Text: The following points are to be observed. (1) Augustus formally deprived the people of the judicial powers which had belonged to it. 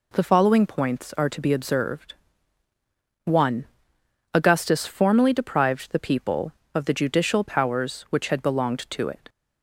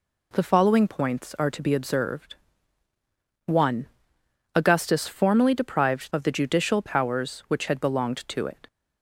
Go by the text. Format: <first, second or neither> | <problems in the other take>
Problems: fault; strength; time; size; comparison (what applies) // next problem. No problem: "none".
first | skips "the people"; at 6.1 s